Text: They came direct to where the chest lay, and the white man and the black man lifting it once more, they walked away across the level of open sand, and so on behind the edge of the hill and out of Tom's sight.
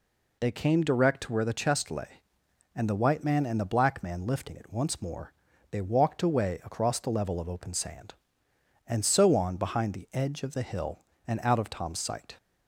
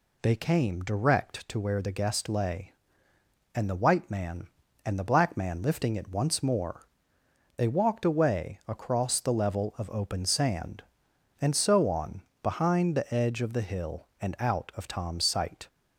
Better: first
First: none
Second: says "guest" for "chest"; at 1.9 s // pauses between "on" and "behind"; slight; at 12.2 s; 0.20 s long

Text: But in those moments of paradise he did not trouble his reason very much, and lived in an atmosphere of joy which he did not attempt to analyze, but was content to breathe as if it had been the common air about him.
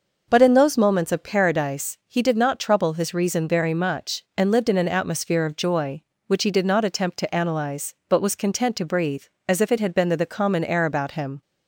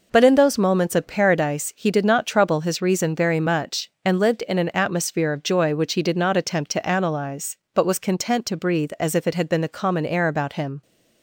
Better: second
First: says "the" twice; at 10.1 s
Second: none

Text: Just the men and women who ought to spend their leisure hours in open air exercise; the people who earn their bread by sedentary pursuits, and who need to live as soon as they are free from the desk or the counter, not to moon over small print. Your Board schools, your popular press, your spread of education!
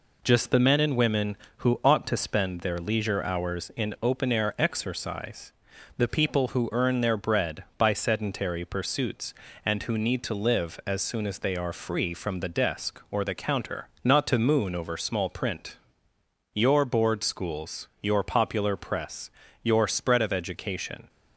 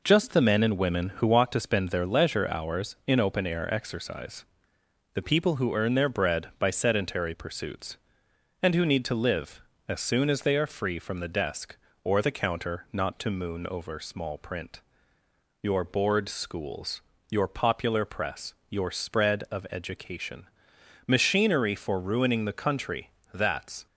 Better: first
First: none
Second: goes on to say "Machinery for ruining the country that's"; strong; from 21.0 s on; 2.8 s long

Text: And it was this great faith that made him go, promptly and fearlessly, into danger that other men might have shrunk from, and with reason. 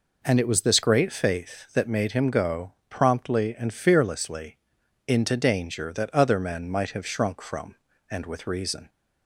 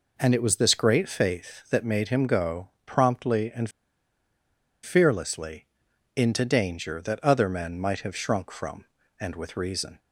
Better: first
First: none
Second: pauses between "and" and "fearlessly"; at 3.6 s; 1.1 s long

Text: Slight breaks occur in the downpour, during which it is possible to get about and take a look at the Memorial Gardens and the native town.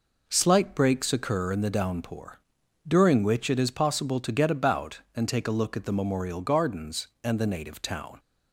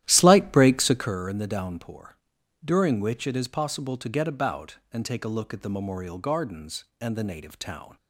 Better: first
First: none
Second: starts louder than the rest; strong; until 1.2 s; 13 dB

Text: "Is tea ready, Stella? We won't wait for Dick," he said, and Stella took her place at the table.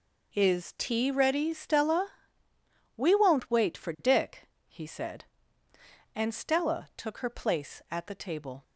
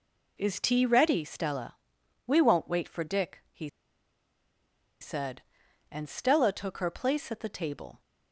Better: first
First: none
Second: pauses between "he" and "said"; strong; at 3.6 s; 1.3 s long

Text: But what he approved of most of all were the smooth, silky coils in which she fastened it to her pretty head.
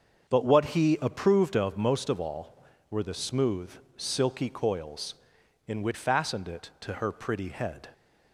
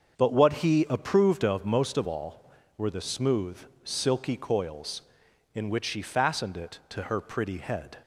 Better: second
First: starts louder than the rest; until 1.3 s; 7 dB // skips "she"; at 5.9 s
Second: starts louder than the rest; until 1.2 s; 7 dB

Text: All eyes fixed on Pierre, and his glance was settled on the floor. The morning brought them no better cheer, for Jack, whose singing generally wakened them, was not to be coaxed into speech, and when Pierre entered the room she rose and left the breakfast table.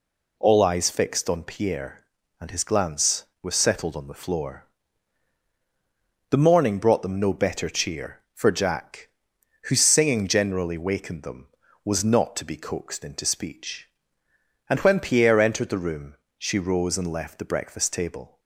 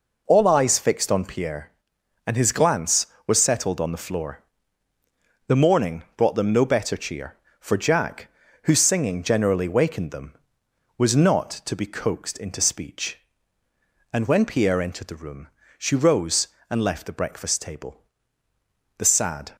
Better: first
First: pauses between "room" and "she"; slight; at 16.1 s; 0.22 s long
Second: pauses between "room" and "she"; slight; at 15.4 s; 0.30 s long // goes on to say "The sad"; from 18.9 s on; 0.58 s long

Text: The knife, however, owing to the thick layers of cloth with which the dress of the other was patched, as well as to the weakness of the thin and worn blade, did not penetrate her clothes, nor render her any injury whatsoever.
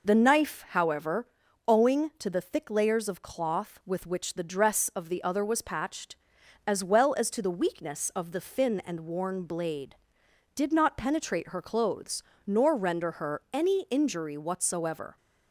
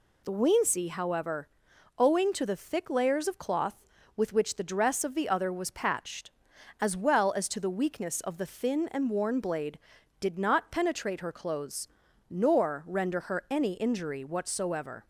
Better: first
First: none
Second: says "weensy" for "knife"; at 0.3 s

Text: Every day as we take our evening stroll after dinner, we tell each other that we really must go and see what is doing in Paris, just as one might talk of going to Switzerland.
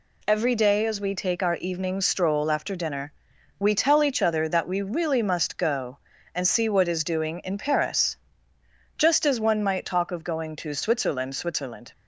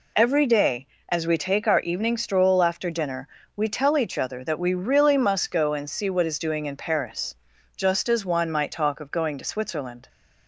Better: second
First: says "Switzerland" twice; at 11.3 s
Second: none

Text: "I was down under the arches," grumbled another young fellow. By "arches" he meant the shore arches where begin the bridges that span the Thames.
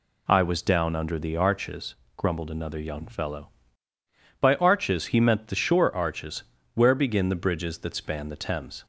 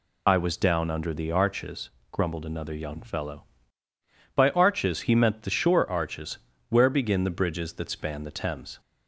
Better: first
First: pauses between "arches" and "where"; slight; at 6.4 s; 0.32 s long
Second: loses the start of "I"; at 0.2 s; 40 ms // pauses between "arches" and "where"; slight; at 6.3 s; 0.32 s long

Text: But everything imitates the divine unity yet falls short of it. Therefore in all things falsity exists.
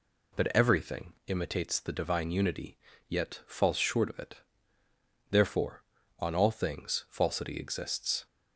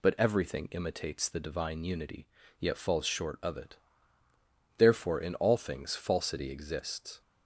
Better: second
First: pauses between "unity" and "yet"; slight; at 2.7 s; 0.30 s long // says "on" for "in"; at 6.1 s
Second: pauses between "unity" and "yet"; slight; at 2.2 s; 0.32 s long

